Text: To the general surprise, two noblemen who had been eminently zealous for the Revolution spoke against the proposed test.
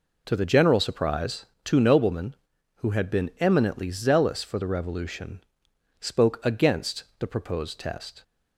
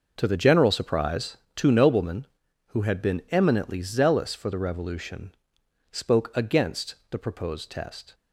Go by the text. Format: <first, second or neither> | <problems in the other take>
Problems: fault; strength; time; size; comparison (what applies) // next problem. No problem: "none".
first | gets quieter; strong; throughout; 13 dB // pauses between "Revolution" and "spoke"; noticeable; at 5.3 s; 0.56 s long; noticeable in the first // pauses between "against" and "the"; slight; at 6.9 s; 0.16 s long; slight in the first